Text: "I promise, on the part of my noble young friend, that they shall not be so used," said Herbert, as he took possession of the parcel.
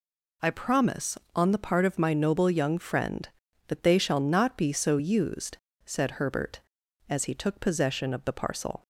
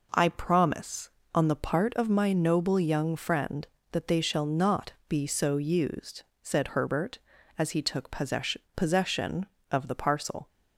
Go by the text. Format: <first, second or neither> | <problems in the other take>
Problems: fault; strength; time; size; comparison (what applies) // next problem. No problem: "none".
first | says "possession" twice; at 8.7 s